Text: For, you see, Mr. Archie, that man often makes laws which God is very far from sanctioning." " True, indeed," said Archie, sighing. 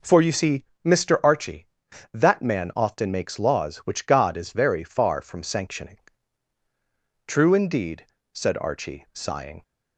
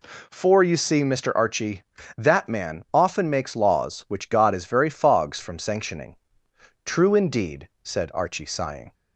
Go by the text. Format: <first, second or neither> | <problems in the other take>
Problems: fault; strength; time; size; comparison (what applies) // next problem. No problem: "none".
first | says "fogs" for "far"; at 4.8 s